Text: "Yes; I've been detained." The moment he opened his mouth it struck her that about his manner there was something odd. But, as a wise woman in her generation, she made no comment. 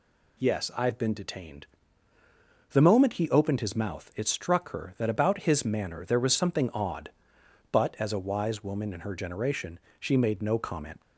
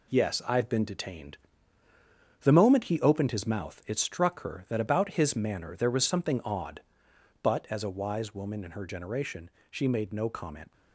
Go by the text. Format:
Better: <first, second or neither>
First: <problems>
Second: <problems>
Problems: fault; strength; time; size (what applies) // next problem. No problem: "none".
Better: first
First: none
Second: gets quieter; throughout; 6.5 dB